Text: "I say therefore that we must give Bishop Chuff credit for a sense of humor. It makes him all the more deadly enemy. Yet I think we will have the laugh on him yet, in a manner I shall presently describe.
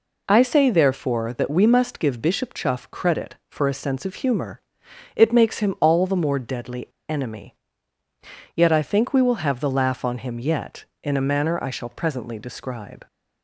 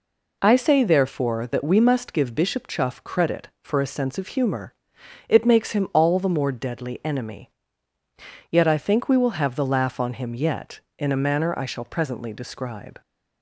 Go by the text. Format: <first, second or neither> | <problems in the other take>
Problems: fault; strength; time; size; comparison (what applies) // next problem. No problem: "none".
second | pauses between "deadly" and "enemy"; slight; at 6.8 s; 0.22 s long